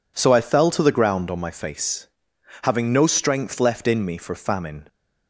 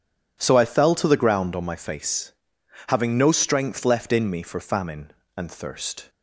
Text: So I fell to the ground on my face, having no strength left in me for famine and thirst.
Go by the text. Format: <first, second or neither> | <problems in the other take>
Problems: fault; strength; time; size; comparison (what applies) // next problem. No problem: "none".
second | stops before "and thirst"; at 4.8 s